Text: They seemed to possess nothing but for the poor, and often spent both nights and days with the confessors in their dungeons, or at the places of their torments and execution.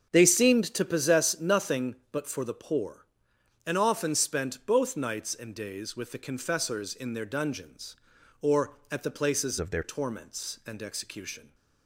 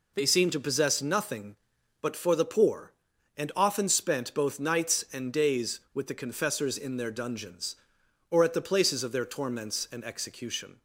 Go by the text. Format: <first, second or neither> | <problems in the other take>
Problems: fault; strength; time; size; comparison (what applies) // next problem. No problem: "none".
second | starts louder than the rest; strong; until 1.1 s; 8 dB // changes voice from "of" to "their"; from 9.5 to 9.8 s; 0.3 s long